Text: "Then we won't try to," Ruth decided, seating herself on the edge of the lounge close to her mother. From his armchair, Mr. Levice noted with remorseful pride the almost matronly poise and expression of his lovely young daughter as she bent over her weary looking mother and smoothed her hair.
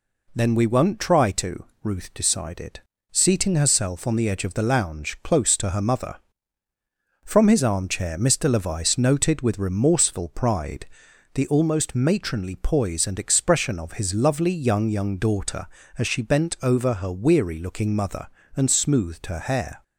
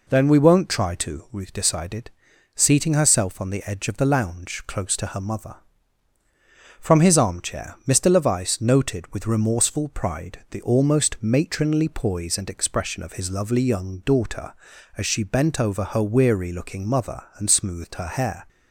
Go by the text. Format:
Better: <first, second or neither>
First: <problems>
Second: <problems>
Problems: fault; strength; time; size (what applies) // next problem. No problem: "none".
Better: second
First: pauses between "pride" and "the"; noticeable; at 10.8 s; 0.48 s long // says "young" twice; at 14.8 s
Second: none